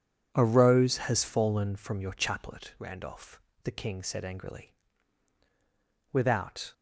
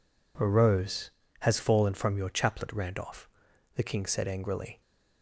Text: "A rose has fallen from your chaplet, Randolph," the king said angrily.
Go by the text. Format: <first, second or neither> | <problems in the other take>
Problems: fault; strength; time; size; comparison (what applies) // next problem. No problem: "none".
second | goes on to say "Without"; noticeable; from 6.1 s on; 0.62 s long